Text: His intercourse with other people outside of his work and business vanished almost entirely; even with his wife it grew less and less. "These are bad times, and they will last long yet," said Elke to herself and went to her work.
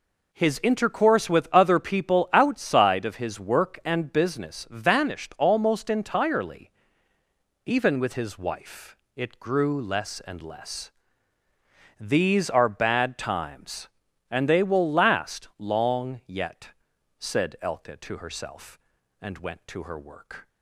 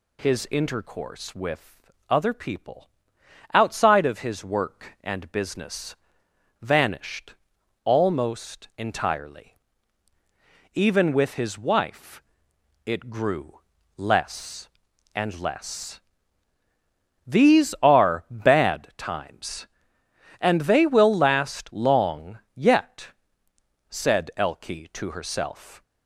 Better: first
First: pauses between "wife" and "it"; slight; at 8.9 s; 0.18 s long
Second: pauses between "with" and "other"; slight; at 1.8 s; 0.20 s long // pauses between "people" and "outside"; noticeable; at 2.8 s; 0.64 s long // pauses between "business" and "vanished"; noticeable; at 5.9 s; 0.64 s long // pauses between "vanished" and "almost"; noticeable; at 7.3 s; 0.50 s long // pauses between "wife" and "it"; noticeable; at 12.2 s; 0.62 s long // pauses between "grew" and "less"; slight; at 13.5 s; 0.36 s long // stops before "and went to her work"; at 25.8 s

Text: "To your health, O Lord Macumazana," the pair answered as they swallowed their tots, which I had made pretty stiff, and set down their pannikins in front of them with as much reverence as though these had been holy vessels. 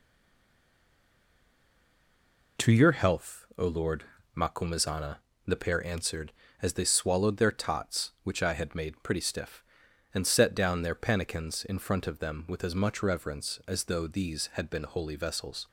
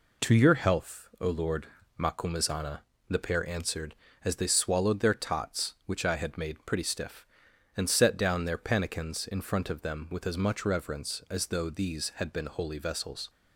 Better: second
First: stays silent before the first word; strong; until 2.5 s; 2.5 s long // pauses between "Lord" and "Macumazana"; slight; at 4.0 s; 0.30 s long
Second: pauses between "Lord" and "Macumazana"; slight; at 1.6 s; 0.30 s long

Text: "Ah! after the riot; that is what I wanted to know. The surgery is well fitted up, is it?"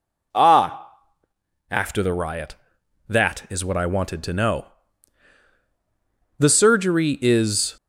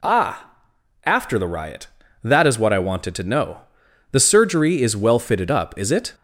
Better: second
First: stops before "well fitted up is it"; at 7.7 s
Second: none

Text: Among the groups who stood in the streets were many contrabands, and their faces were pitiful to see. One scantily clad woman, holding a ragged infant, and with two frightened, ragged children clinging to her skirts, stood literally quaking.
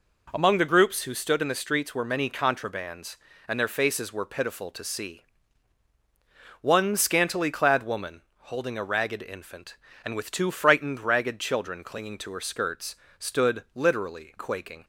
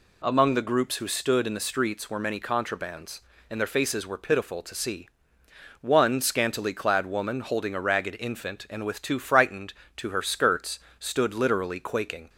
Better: first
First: none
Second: skips "ragged children clinging"; at 9.8 s

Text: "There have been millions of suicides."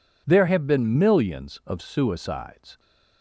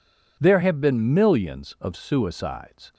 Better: neither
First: none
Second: none

